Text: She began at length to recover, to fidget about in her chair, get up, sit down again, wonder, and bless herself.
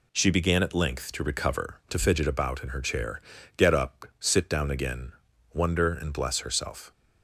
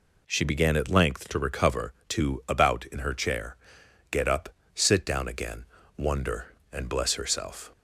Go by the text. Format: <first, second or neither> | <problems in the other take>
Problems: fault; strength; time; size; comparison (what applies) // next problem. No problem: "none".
first | skips "fidget"; at 2.4 s